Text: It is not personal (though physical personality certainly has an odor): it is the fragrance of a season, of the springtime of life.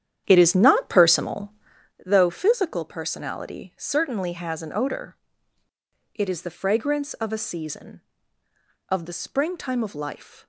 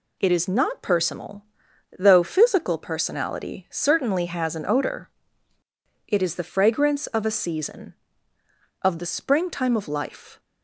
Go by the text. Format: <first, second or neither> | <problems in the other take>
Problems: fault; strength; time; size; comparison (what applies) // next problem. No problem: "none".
second | starts louder than the rest; strong; until 1.9 s; 10 dB